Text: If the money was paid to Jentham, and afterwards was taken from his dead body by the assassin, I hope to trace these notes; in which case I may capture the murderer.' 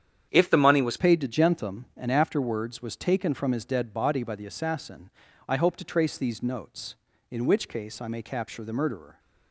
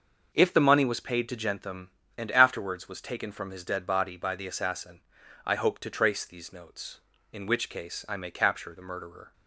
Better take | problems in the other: second | starts louder than the rest; strong; until 1.3 s; 9 dB; noticeable in the second // changes voice at "paid"; from 0.9 s on; 8.2 s long

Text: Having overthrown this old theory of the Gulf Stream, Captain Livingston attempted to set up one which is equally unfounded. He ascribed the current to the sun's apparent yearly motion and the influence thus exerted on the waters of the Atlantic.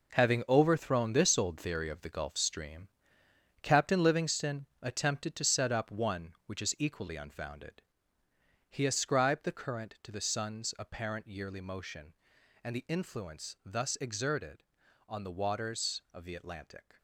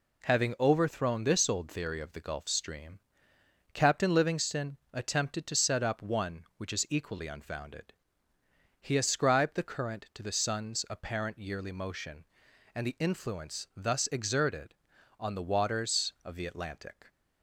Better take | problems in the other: second | gets quieter; strong; throughout; 10 dB // pauses between "Livingston" and "attempted"; slight; at 4.6 s; 0.16 s long; slight in the second

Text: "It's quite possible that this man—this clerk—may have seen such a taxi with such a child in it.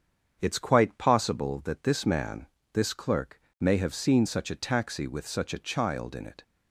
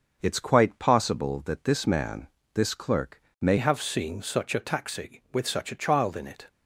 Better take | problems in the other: first | starts louder than the rest; until 1.2 s; 6.5 dB; strong in the first // changes voice at "have"; from 3.5 s on; 2.9 s long

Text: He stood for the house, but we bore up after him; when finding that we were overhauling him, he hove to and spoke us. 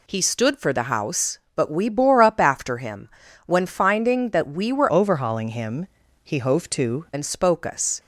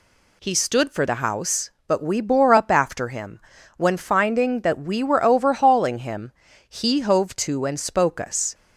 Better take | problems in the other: second | changes voice from "overhauling" to "to"; from 4.9 to 7.0 s; 2.1 s long

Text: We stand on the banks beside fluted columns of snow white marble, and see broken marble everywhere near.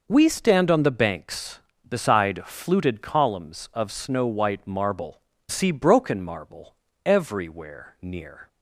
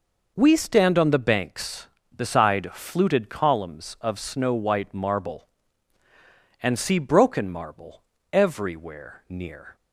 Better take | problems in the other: second | skips "and"; at 5.3 s // pauses between "marble" and "everywhere"; slight; at 6.7 s; 0.30 s long; slight in the second

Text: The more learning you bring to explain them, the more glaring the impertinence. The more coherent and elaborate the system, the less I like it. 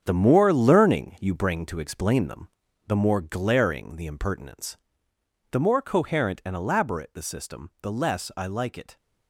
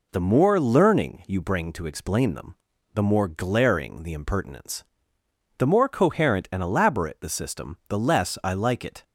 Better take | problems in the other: second | gets quieter; strong; throughout; 9.5 dB

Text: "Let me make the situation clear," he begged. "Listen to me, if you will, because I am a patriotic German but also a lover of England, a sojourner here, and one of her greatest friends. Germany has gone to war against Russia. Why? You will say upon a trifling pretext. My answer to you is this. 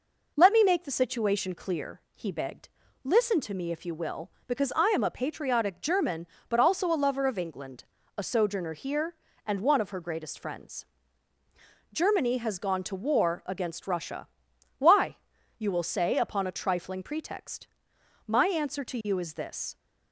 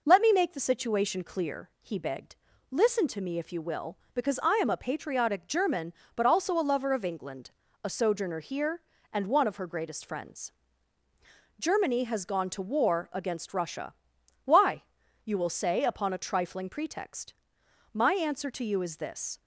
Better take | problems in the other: neither | none

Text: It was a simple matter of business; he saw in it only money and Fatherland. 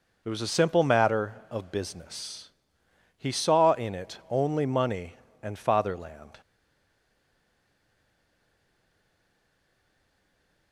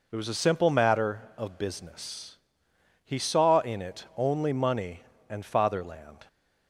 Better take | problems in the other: second | stays silent after the last word; strong; from 6.4 s on; 4.3 s long

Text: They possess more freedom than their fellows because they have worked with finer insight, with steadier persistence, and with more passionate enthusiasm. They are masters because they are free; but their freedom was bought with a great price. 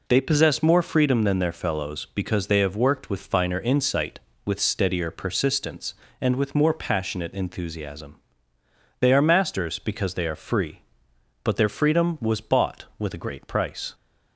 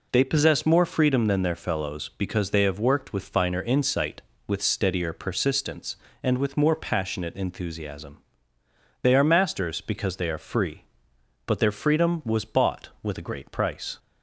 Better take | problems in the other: neither | none

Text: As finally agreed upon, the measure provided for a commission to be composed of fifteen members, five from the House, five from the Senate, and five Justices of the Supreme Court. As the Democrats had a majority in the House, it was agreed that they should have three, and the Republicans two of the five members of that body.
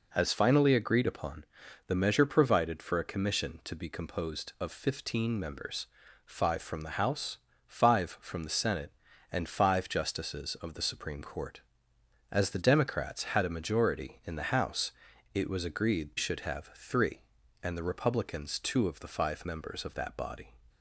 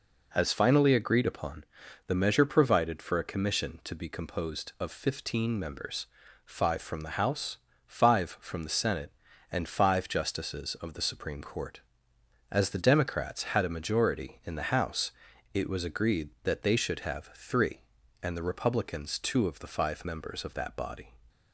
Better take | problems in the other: second | skips "that they"; at 16.1 s

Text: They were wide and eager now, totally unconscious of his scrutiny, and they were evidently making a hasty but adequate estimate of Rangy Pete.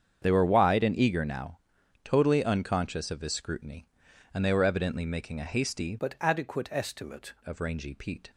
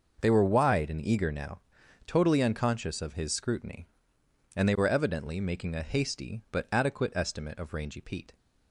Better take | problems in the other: second | starts louder than the rest; strong; until 1.2 s; 7.5 dB // changes voice from "but" to "estimate"; from 5.9 to 7.3 s; 1.4 s long

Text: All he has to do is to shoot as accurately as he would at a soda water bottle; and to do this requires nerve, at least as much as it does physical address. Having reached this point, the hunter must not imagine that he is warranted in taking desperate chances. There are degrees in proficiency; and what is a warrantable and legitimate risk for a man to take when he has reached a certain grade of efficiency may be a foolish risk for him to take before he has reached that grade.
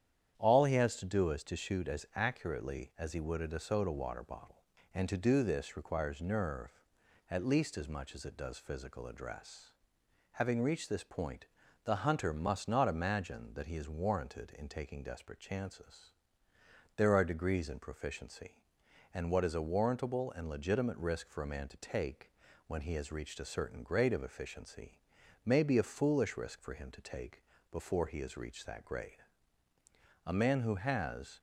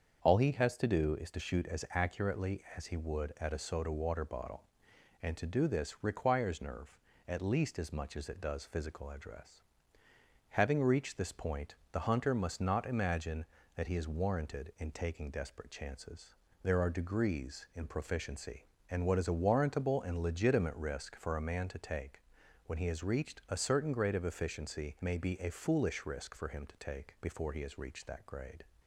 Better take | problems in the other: second | starts louder than the rest; strong; until 1.3 s; 9.5 dB; strong in the second // pauses between "take" and "when"; at 22.2 s; 0.38 s long; also in the second // pauses between "efficiency" and "may"; noticeable; at 24.9 s; 0.46 s long // pauses between "take" and "before"; slight; at 27.4 s; 0.30 s long // goes on to say "A man who has"; noticeable; from 30.2 s on; 1.1 s long

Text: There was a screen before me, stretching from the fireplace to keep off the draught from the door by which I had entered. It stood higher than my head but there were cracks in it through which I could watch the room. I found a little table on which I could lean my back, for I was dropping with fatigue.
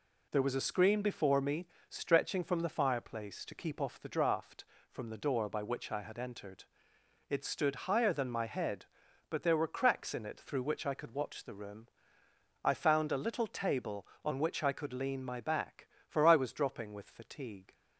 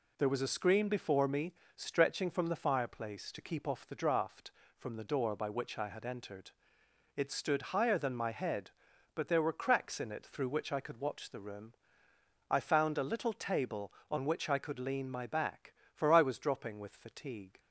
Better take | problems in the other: neither | none

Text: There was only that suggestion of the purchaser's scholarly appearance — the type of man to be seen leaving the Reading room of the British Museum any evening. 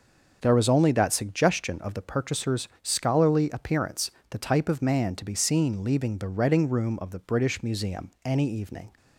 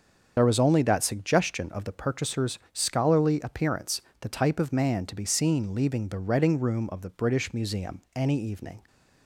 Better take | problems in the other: first | loses the start of "There"; at 0.3 s; 45 ms // starts louder than the rest; until 1.3 s; 7 dB

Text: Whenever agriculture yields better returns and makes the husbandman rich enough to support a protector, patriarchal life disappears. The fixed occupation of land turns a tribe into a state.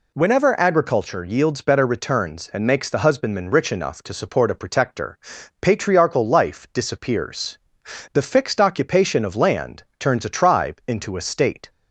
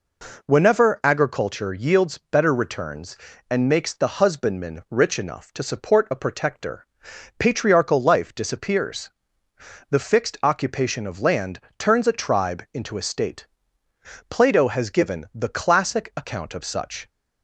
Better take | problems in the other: first | pauses between "land" and "turns"; slight; at 11.5 s; 0.18 s long // goes on to say "Plato has given the classic account of such"; strong; from 14.3 s on; 2.7 s long

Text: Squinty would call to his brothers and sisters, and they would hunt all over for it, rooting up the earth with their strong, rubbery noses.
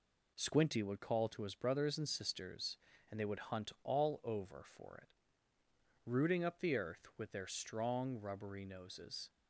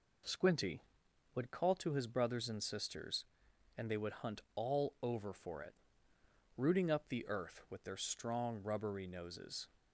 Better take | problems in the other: neither | none

